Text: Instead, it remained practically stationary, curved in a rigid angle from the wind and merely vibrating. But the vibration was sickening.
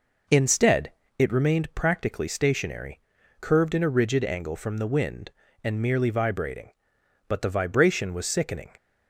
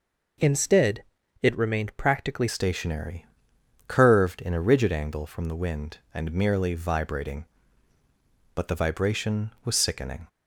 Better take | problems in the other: first | changes voice at "stationary"; from 2.4 s on; 7.8 s long

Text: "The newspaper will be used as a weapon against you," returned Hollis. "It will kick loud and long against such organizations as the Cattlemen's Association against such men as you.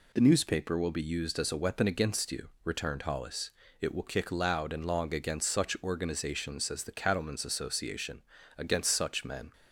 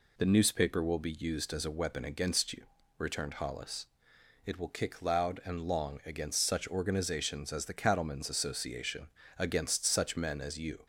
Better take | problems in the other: second | pauses between "Association" and "against"; slight; at 8.2 s; 0.36 s long; slight in the second // stops before "as you"; at 9.5 s

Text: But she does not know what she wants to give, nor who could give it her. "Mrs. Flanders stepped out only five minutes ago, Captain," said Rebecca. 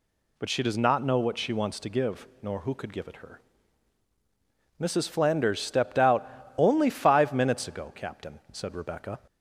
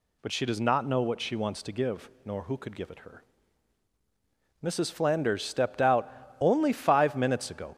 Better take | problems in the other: first | pauses between "out" and "only"; slight; at 6.1 s; 0.30 s long; slight in the first // stops before "Captain said Rebecca"; at 7.7 s

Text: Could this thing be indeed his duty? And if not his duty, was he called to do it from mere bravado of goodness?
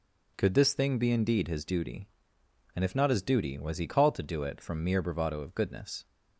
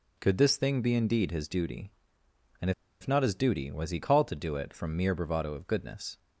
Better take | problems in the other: first | pauses between "And" and "if"; slight; at 2.7 s; 0.29 s long

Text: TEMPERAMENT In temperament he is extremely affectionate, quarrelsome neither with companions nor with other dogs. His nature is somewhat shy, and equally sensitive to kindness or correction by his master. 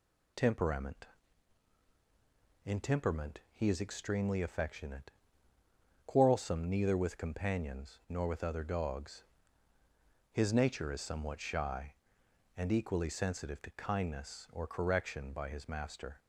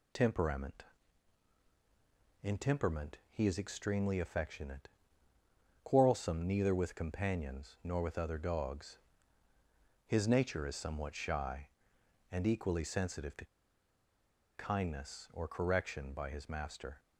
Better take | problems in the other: first | pauses between "to" and "kindness"; at 13.4 s; 1.0 s long

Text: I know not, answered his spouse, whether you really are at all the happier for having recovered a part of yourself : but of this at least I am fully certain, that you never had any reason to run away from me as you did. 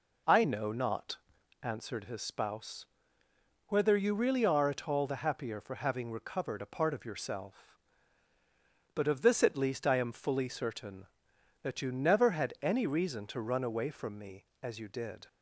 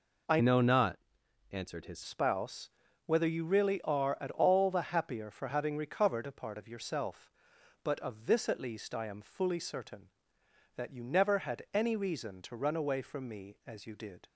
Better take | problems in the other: first | changes voice from "know" to "his"; from 0.4 to 2.0 s; 1.6 s long

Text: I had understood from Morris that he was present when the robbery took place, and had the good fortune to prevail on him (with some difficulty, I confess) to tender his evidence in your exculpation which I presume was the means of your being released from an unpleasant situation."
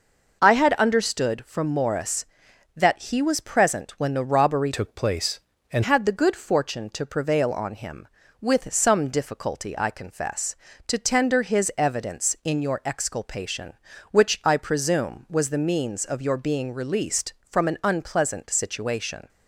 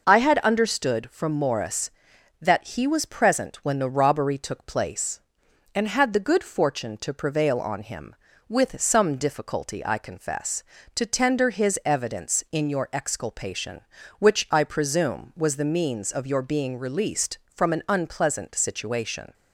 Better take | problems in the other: second | changes voice from "took" to "and"; from 4.7 to 5.8 s; 1.1 s long

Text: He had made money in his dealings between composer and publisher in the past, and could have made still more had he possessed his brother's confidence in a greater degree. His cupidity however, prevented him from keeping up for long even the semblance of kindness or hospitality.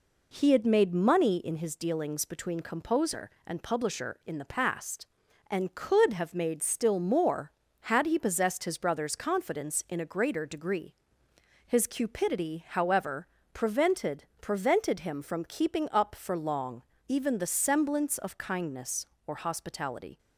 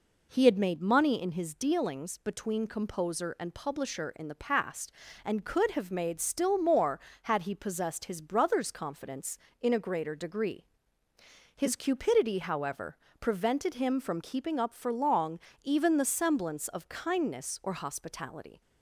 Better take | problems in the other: second | says "prevented" twice; at 14.4 s // pauses between "long" and "even"; slight; at 16.8 s; 0.26 s long; slight in the second

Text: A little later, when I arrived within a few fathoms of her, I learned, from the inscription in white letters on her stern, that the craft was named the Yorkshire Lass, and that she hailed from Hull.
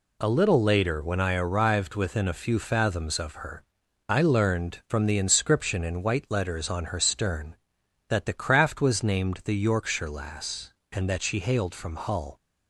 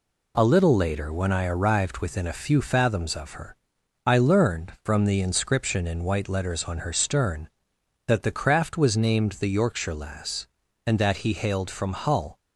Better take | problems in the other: first | says "he" for "she"; at 11.1 s

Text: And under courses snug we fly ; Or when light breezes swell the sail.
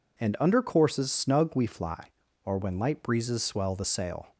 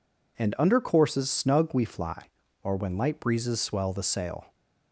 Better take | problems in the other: neither | none

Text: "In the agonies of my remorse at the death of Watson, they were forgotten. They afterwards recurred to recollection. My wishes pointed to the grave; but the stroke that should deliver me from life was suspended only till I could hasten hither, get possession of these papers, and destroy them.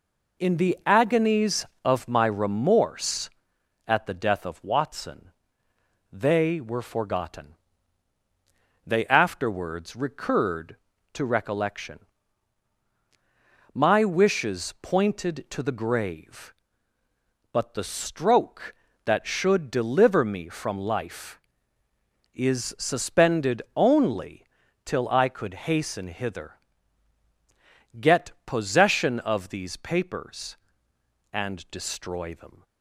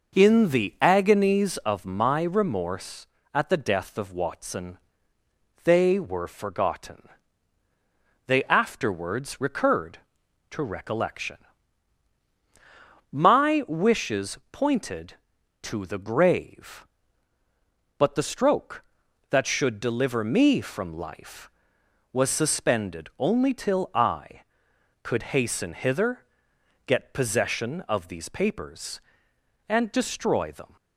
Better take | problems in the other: second | says "is" for "was"; at 22.3 s // pauses between "only" and "till"; at 24.4 s; 0.40 s long

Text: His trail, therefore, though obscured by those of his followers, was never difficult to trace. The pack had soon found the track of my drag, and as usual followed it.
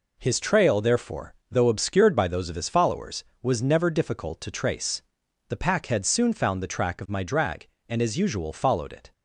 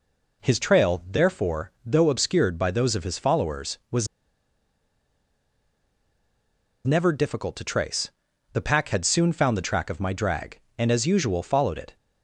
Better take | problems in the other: first | pauses between "was" and "never"; strong; at 4.0 s; 2.7 s long

